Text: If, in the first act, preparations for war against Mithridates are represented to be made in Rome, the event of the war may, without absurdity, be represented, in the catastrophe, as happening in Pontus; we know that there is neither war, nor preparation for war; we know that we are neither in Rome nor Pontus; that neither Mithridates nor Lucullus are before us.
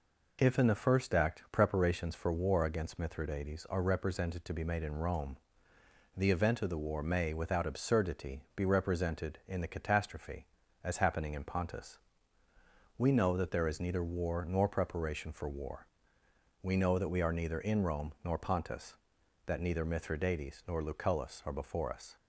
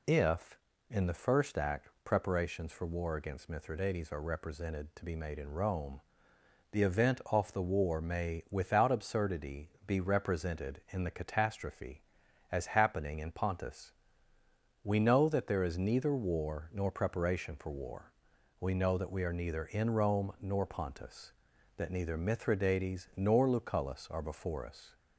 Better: first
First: none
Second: says "off" for "of"; at 7.2 s

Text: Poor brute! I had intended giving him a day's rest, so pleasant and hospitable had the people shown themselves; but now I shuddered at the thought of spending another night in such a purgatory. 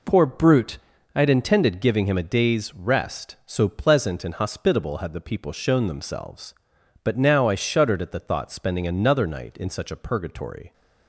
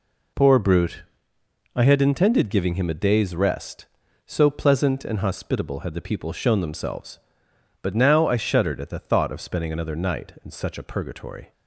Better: second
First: skips "of"; at 8.5 s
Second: none

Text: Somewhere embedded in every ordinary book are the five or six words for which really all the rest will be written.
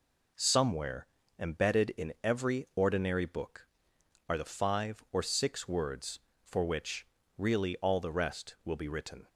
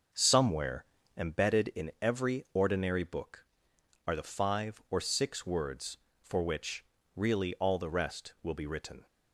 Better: first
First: pauses between "Somewhere" and "embedded"; slight; at 1.0 s; 0.32 s long // pauses between "which" and "really"; slight; at 7.0 s; 0.32 s long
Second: starts louder than the rest; until 1.3 s; 6.5 dB // pauses between "Somewhere" and "embedded"; slight; at 0.8 s; 0.32 s long // pauses between "which" and "really"; slight; at 6.8 s; 0.32 s long

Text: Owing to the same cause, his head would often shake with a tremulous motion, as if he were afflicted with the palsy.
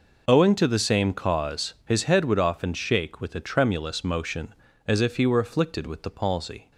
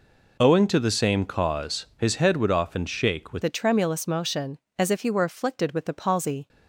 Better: first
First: none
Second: changes voice at "a"; from 3.4 s on; 3.0 s long

